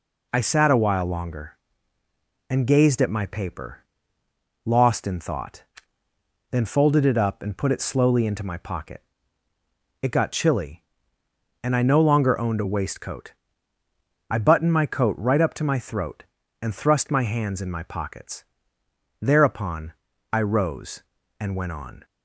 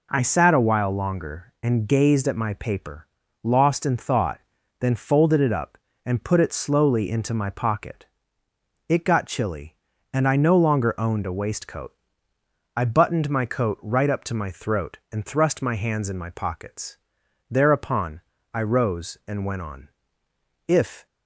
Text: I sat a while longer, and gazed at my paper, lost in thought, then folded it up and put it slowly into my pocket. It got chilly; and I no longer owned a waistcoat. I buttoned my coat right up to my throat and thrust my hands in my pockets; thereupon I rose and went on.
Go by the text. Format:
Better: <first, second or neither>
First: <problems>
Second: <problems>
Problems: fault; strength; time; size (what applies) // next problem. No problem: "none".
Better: first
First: pauses between "thereupon" and "I"; at 19.9 s; 0.38 s long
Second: pauses between "thereupon" and "I"; slight; at 18.2 s; 0.30 s long // goes on to say "If"; slight; from 20.6 s on; 0.38 s long